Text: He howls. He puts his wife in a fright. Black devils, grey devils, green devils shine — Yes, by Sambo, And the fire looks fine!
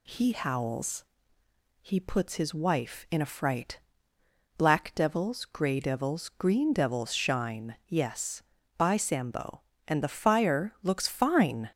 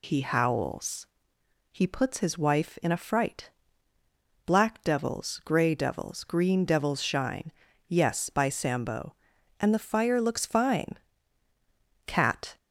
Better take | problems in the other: first | goes on to say "Cat"; from 12.0 s on; 0.52 s long

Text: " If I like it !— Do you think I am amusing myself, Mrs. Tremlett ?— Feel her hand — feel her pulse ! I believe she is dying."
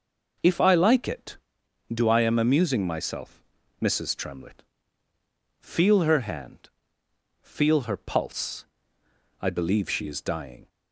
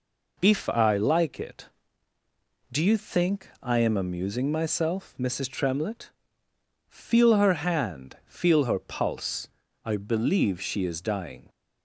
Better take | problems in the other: second | skips "you think"; at 2.0 s

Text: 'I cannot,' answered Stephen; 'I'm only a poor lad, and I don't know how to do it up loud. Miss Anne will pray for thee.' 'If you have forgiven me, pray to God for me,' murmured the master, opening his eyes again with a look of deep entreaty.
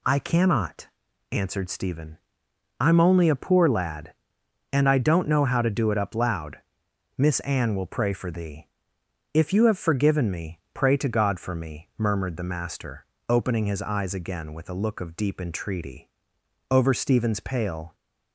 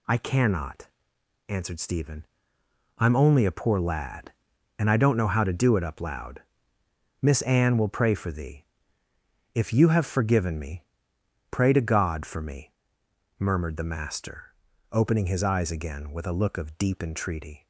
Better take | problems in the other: second | goes on to say "Over Stephen's pale"; noticeable; from 16.6 s on; 1.2 s long

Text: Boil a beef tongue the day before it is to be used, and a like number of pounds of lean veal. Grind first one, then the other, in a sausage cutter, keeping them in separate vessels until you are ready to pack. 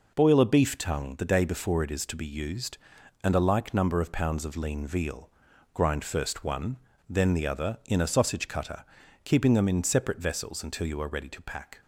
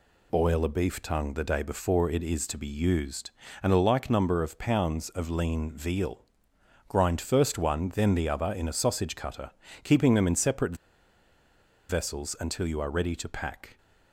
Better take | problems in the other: first | pauses between "separate" and "vessels"; at 10.7 s; 1.1 s long

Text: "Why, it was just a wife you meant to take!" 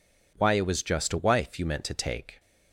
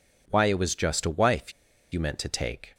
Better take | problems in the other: first | pauses between "wife" and "you"; at 1.5 s; 0.40 s long

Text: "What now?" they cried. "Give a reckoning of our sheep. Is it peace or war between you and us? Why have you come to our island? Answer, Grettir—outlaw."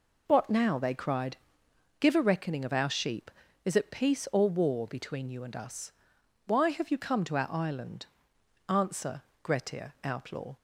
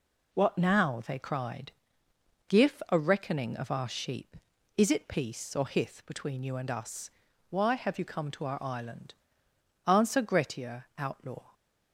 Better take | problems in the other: first | says "hith" for "war"; at 5.6 s

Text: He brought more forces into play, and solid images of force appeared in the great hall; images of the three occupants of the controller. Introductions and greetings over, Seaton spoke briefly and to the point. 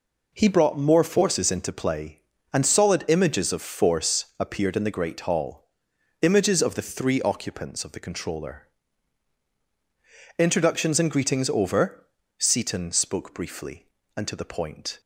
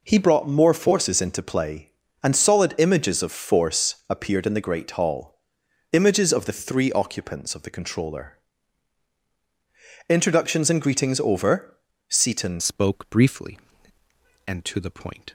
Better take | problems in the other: first | changes voice at "spoke"; from 12.5 s on; 2.8 s long

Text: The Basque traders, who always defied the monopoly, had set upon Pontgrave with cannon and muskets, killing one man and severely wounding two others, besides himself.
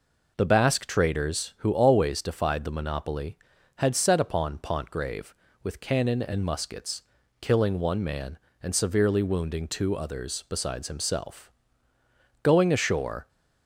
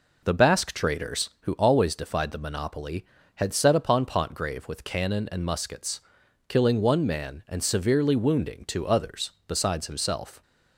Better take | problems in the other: second | goes on to say "Going ashore"; noticeable; from 12.4 s on; 0.86 s long

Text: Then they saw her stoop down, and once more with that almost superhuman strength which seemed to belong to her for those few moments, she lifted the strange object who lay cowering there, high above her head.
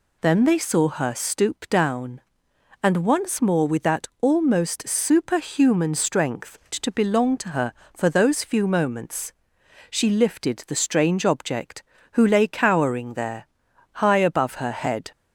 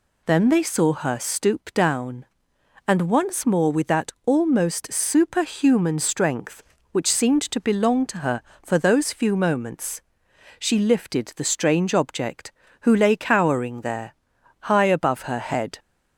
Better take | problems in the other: second | skips "which seemed"; at 6.6 s

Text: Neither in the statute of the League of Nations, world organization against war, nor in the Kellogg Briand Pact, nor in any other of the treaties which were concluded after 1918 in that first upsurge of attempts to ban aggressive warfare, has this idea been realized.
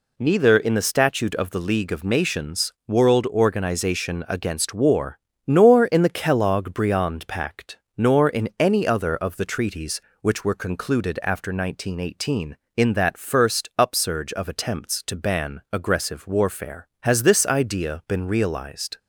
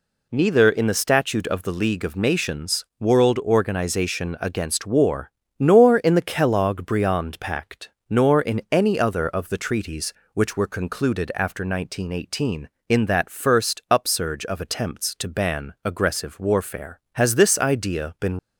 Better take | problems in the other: first | stops before "realized"; at 18.3 s

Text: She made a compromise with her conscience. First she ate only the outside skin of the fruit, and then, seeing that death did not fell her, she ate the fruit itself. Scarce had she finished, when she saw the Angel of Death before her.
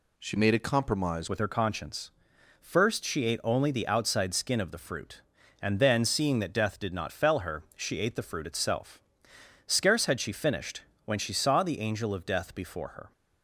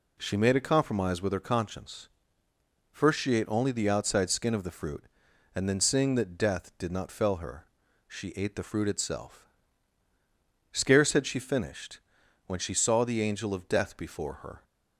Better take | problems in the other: second | changes voice at "with"; from 1.2 s on; 11.9 s long

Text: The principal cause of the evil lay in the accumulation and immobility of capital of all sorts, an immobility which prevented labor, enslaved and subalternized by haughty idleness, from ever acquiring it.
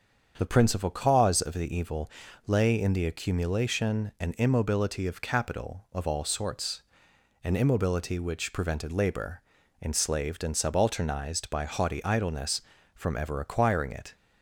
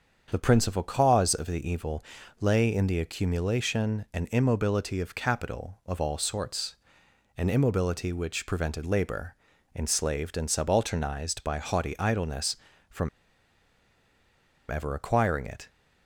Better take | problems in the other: first | starts louder than the rest; strong; until 1.3 s; 7.5 dB; strong in the first // pauses between "evil" and "lay"; slight; at 2.0 s; 0.36 s long; slight in the first // pauses between "from" and "ever"; strong; at 13.0 s; 1.6 s long

